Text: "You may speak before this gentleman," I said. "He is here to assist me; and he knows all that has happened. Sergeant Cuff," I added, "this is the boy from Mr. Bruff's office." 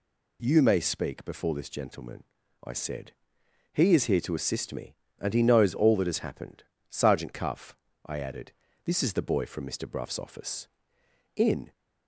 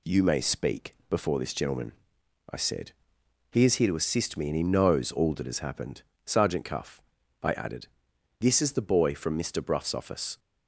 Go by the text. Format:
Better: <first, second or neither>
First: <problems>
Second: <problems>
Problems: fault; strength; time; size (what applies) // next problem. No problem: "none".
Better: second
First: goes on to say "In"; slight; from 11.3 s on; 0.36 s long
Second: none